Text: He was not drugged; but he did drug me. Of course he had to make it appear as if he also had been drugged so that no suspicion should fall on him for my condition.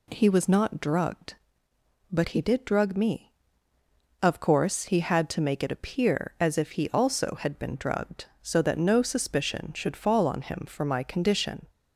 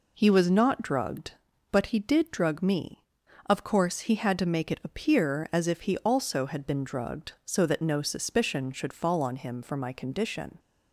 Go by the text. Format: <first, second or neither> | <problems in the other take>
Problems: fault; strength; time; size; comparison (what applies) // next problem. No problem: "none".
neither | none